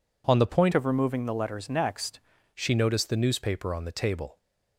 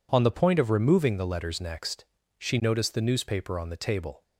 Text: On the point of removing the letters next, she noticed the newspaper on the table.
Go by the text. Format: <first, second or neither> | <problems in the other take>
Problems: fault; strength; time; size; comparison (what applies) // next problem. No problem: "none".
second | changes voice from "of" to "next"; from 0.7 to 2.1 s; 1.4 s long